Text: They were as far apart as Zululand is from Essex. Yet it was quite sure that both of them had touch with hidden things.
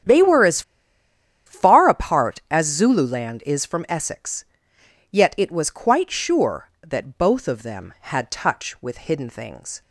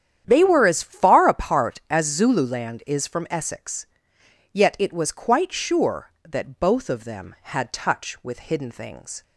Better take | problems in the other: second | starts louder than the rest; strong; until 1.9 s; 9.5 dB; strong in the second // pauses between "as" and "far"; noticeable; at 0.6 s; 0.85 s long

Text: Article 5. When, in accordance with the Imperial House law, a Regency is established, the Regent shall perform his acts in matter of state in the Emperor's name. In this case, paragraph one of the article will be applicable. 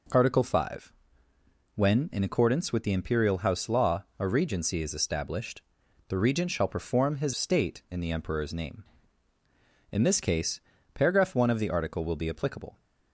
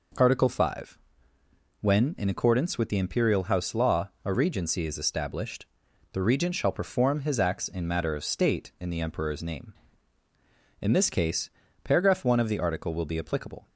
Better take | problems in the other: second | skips "acts in matter of"; at 7.3 s

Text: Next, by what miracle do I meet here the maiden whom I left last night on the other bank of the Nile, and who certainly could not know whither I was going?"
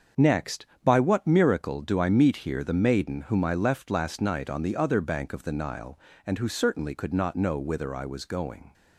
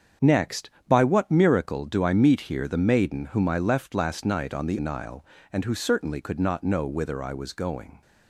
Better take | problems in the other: first | starts louder than the rest; strong; until 1.4 s; 7.5 dB; also in the first // skips "other bank of the"; at 4.7 s

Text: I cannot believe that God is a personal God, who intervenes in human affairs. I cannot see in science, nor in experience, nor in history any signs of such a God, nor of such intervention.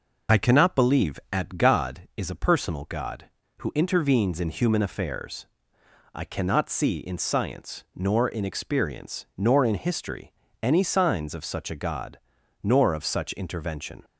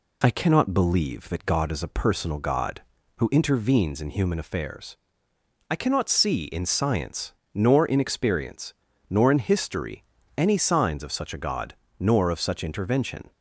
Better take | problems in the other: second | says "at" for "that"; at 1.3 s // pauses between "history" and "any"; slight; at 10.3 s; 0.32 s long; slight in the second

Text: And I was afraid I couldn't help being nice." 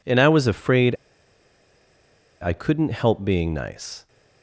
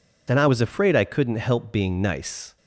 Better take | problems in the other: second | pauses between "afraid" and "I"; strong; at 0.9 s; 1.4 s long

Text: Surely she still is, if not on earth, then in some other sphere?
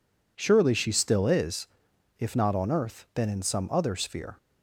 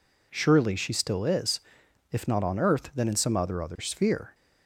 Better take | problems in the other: first | says "other" twice; at 3.6 s

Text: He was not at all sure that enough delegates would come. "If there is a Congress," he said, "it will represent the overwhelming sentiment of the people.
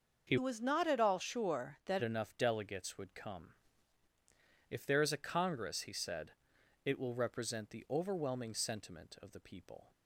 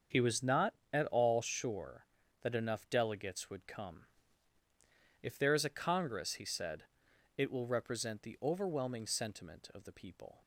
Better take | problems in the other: second | starts louder than the rest; until 1.2 s; 6 dB; also in the second // changes voice from "was" to "that"; from 0.3 to 2.0 s; 1.7 s long

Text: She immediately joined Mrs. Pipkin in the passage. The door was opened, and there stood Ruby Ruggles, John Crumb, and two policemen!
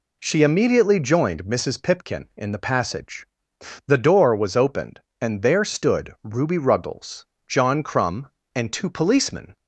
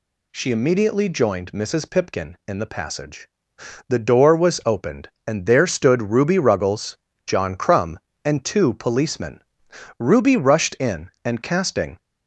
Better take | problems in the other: first | goes on to say "Ruby rushed in and casting"; strong; from 9.9 s on; 2.0 s long

